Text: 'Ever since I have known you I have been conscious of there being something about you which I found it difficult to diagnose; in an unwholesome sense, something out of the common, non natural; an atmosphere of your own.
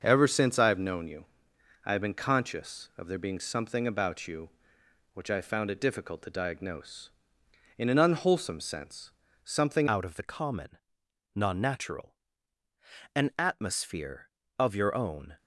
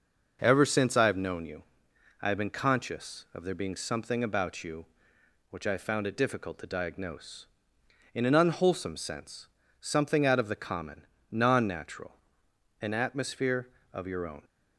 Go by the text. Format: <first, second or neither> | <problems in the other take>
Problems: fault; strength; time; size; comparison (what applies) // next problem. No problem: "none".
second | starts louder than the rest; until 1.0 s; 6.5 dB // pauses between "you" and "I"; noticeable; at 1.2 s; 0.58 s long; noticeable in the second // changes voice at "out"; from 9.8 s on; 5.5 s long